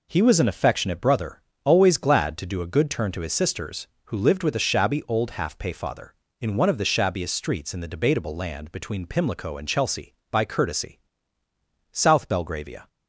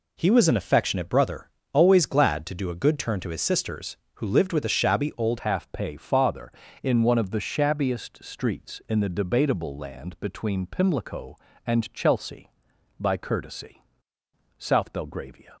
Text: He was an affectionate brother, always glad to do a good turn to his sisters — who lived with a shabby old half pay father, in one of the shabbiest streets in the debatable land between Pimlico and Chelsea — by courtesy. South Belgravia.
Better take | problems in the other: first | changes voice at "half"; from 5.4 s on; 10.1 s long

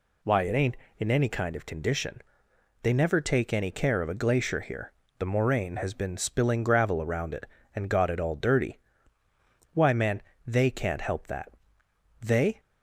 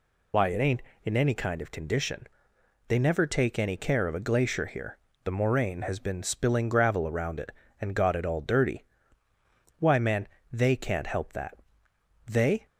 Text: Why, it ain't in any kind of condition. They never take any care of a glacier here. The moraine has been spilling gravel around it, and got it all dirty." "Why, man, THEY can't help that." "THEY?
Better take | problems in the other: first | loses the start of "Why"; at 0.3 s; 50 ms

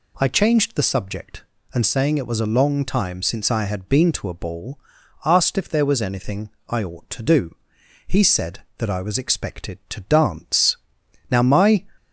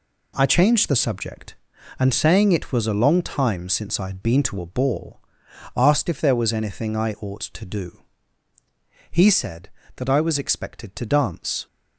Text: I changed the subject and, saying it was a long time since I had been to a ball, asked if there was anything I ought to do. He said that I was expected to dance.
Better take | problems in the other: second | pauses between "anything" and "I"; slight; at 6.4 s; 0.20 s long // goes on to say "Now my"; from 11.2 s on; 0.56 s long

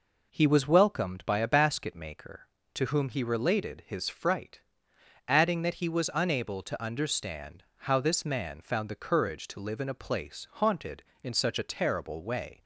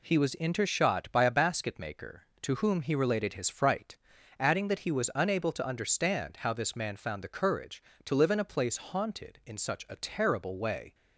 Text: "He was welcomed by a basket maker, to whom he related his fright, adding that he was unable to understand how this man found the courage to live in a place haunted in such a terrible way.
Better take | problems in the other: first | says "intershot" for "welcomed"; at 0.3 s

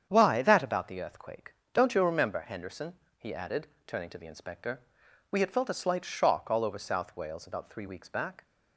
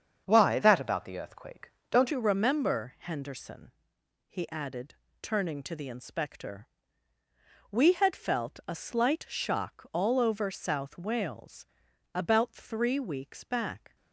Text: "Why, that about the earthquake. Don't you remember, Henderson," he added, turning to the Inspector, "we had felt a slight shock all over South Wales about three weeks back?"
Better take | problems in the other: first | starts louder than the rest; strong; until 1.2 s; 7.5 dB; strong in the first // changes voice at "you"; from 2.1 s on; 11.8 s long // pauses between "Wales" and "about"; noticeable; at 11.6 s; 0.50 s long

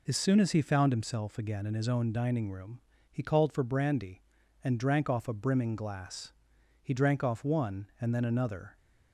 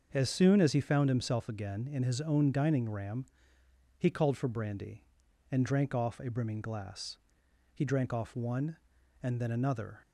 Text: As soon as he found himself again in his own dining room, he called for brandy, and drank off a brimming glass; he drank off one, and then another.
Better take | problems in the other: first | starts louder than the rest; until 1.1 s; 6.5 dB // says "ram" for "room"; at 2.8 s

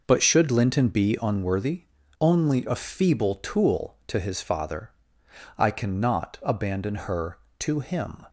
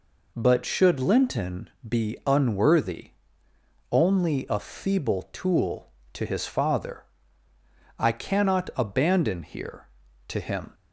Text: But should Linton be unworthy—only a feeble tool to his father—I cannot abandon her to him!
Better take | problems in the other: first | pauses between "Linton" and "be"; slight; at 1.6 s; 0.18 s long // says "here" for "her"; at 9.4 s

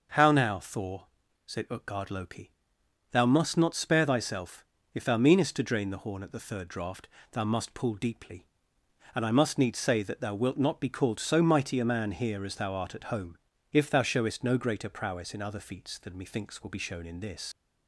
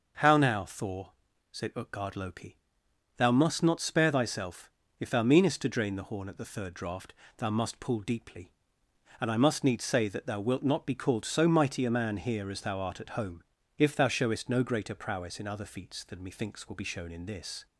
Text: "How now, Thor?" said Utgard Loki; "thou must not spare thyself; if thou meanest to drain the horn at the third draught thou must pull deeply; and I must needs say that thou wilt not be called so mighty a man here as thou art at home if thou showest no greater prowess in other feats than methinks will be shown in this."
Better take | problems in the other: second | starts louder than the rest; noticeable; until 1.5 s; 6 dB; noticeable in the second // pauses between "draught" and "thou"; slight; at 7.0 s; 0.24 s long; slight in the second // pauses between "home" and "if"; slight; at 13.3 s; 0.34 s long; slight in the second // leaves "this" unfinished; at 17.5 s; 85 ms

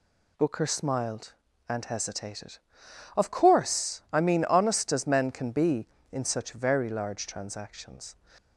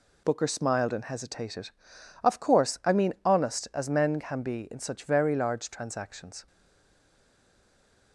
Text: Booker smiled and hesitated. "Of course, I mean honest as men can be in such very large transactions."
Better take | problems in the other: first | stays silent after the last word; noticeable; from 6.4 s on; 1.7 s long

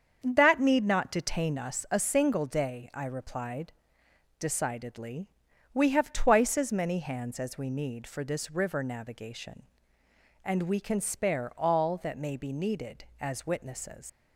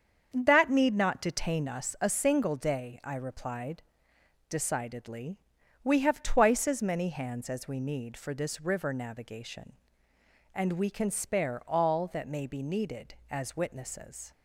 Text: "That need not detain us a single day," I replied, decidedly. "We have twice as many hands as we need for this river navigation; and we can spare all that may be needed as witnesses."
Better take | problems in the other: second | starts louder than the rest; strong; until 1.2 s; 7.5 dB; strong in the second // leaves "witnesses" unfinished; at 14.0 s; 120 ms

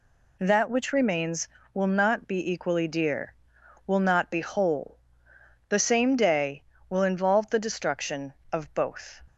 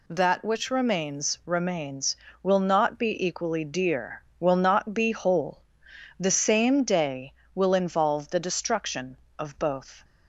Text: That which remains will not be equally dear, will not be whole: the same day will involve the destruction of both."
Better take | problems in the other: first | says "remains" twice; at 1.4 s

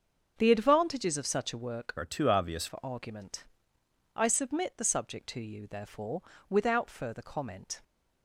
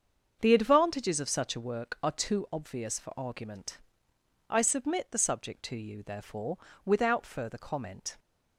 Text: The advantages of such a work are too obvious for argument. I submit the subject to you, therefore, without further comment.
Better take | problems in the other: second | starts louder than the rest; until 1.3 s; 7 dB; also in the second // changes voice from "are" to "obvious"; from 1.9 to 2.6 s; 0.7 s long

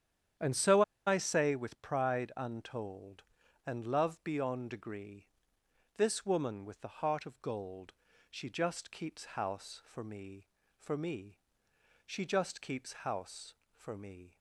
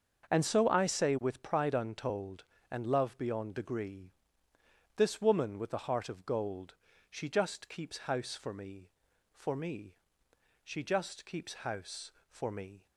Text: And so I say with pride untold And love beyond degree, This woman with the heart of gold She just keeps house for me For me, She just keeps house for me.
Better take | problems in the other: second | starts louder than the rest; strong; until 1.6 s; 9.5 dB; also in the second // pauses between "so" and "I"; slight; at 0.8 s; 0.25 s long // pauses between "gold" and "She"; at 7.9 s; 0.38 s long; slight in the second

